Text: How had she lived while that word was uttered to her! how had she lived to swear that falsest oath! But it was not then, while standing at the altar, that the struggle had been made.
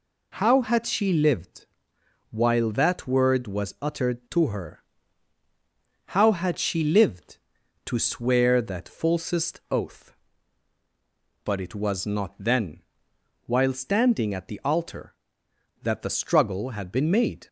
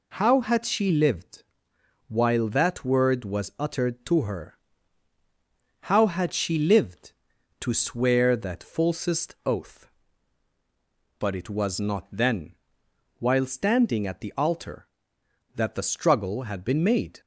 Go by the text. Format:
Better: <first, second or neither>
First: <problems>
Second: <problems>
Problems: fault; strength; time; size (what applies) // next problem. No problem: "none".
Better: neither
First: pauses between "lived" and "while"; noticeable; at 1.6 s; 0.64 s long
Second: pauses between "lived" and "while"; noticeable; at 1.4 s; 0.64 s long